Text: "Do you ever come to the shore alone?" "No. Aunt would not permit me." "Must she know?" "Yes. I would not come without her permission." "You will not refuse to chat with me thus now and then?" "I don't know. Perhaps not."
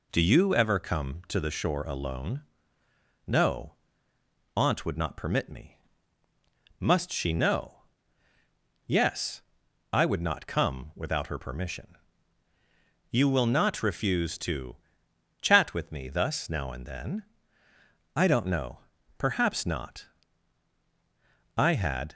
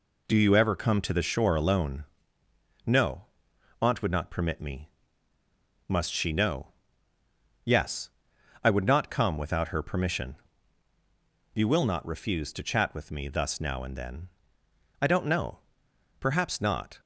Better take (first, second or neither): second